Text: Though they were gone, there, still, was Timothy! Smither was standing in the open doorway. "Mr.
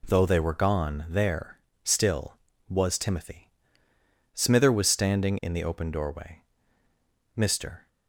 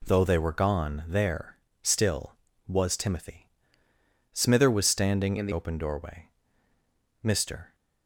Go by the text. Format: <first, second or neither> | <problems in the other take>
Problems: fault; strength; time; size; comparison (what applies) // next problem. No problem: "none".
first | changes voice from "in" to "the"; from 5.3 to 5.5 s; 0.2 s long